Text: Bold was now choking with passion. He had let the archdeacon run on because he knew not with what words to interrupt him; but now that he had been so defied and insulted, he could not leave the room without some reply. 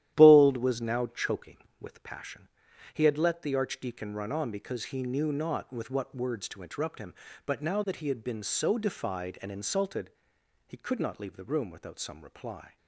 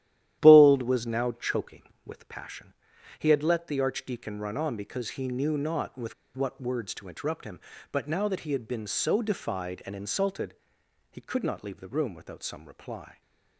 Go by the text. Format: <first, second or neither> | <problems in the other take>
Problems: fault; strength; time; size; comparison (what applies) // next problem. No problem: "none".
first | starts louder than the rest; strong; until 1.4 s; 12 dB; strong in the first // pauses between "with" and "what"; slight; at 6.1 s; 0.22 s long